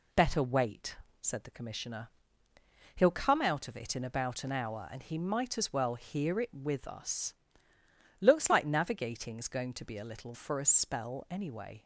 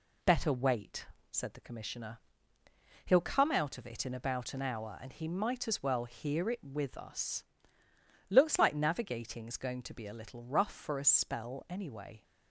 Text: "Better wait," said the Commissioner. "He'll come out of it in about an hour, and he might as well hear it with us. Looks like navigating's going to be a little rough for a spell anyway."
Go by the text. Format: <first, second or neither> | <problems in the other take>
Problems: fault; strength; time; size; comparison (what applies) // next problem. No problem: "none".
second | skips "rough"; at 10.3 s